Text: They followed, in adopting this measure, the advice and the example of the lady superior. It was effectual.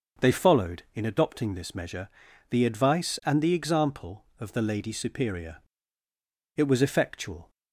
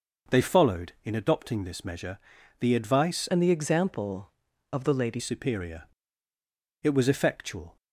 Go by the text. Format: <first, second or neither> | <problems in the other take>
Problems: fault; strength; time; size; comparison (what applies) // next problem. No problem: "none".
first | changes voice from "and" to "lady"; from 3.2 to 5.1 s; 1.9 s long